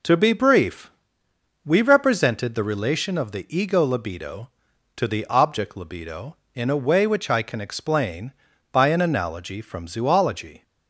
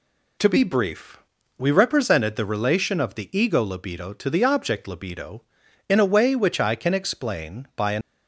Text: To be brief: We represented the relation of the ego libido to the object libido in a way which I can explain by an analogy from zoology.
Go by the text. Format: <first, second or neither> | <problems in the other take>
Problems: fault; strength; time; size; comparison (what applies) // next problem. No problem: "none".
first | stops before "analogy from zoology"; at 8.0 s